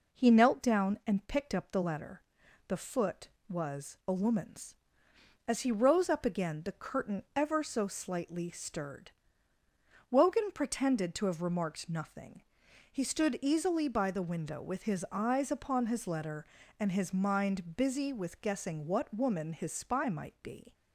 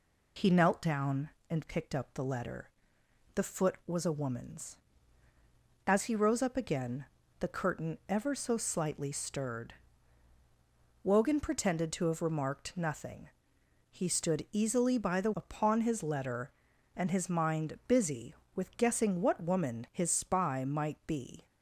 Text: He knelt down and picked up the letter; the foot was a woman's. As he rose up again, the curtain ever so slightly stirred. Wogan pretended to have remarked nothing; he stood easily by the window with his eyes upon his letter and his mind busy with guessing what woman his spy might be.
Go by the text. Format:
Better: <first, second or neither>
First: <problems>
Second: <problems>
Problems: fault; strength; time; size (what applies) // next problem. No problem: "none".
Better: first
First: none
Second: skips "window with his eyes"; at 15.3 s